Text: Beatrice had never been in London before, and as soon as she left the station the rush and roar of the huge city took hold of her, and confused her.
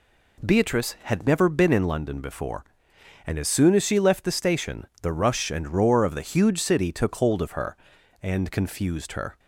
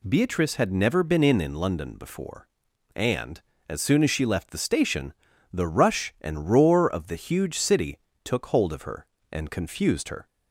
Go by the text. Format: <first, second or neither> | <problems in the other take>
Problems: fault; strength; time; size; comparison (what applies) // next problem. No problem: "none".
first | says "in" twice; at 1.4 s // pauses between "station" and "the"; at 5.1 s; 0.40 s long // pauses between "city" and "took"; slight; at 7.9 s; 0.24 s long